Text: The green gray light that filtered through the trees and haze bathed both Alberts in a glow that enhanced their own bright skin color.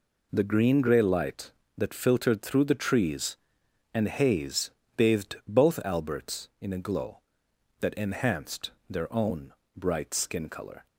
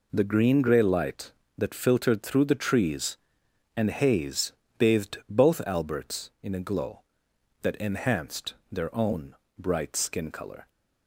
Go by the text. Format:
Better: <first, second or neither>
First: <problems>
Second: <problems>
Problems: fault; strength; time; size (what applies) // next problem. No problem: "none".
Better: neither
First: pauses between "haze" and "bathed"; slight; at 4.7 s; 0.26 s long // pauses between "enhanced" and "their"; slight; at 8.7 s; 0.18 s long // pauses between "own" and "bright"; slight; at 9.5 s; 0.24 s long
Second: pauses between "haze" and "bathed"; slight; at 4.5 s; 0.26 s long // pauses between "enhanced" and "their"; slight; at 8.5 s; 0.17 s long // pauses between "own" and "bright"; slight; at 9.3 s; 0.24 s long